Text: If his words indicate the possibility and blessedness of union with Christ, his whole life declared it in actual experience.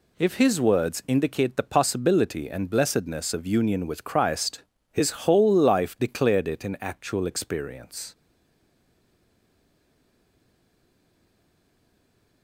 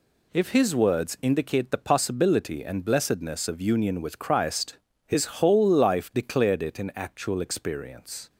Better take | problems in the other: second | pauses between "his" and "whole"; slight; at 5.1 s; 0.16 s long; slight in the second // stays silent after the last word; strong; from 8.1 s on; 4.3 s long

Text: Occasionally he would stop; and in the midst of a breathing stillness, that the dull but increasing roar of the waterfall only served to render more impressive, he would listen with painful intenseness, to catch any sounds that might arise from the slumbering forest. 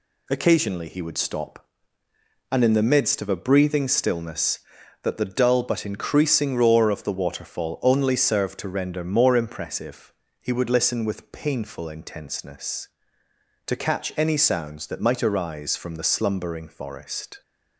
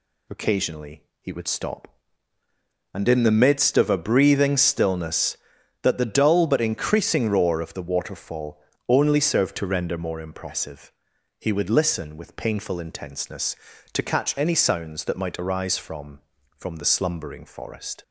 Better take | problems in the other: first | pauses between "Occasionally" and "he"; slight; at 1.0 s; 0.18 s long // pauses between "waterfall" and "only"; slight; at 8.6 s; 0.26 s long // says "from" twice; at 16.5 s

